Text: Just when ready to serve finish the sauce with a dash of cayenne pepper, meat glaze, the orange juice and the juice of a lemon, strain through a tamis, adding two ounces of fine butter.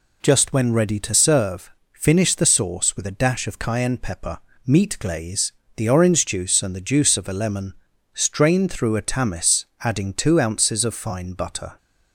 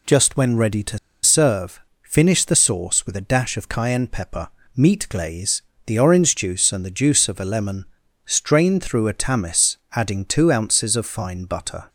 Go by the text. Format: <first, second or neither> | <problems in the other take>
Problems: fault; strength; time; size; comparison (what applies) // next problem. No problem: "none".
first | pauses between "to" and "serve"; slight; at 0.9 s; 0.25 s long // pauses between "serve" and "finish"; slight; at 1.8 s; 0.22 s long; slight in the first